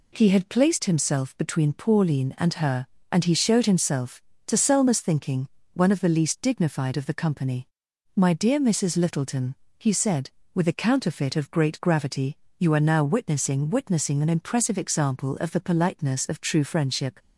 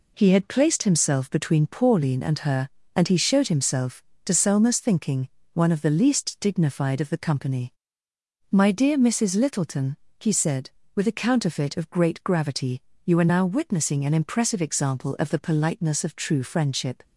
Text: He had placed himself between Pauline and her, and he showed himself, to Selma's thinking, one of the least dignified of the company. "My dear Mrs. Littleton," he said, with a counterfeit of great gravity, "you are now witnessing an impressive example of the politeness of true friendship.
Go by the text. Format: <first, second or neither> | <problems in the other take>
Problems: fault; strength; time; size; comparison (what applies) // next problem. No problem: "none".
second | says "witnessing" twice; at 13.7 s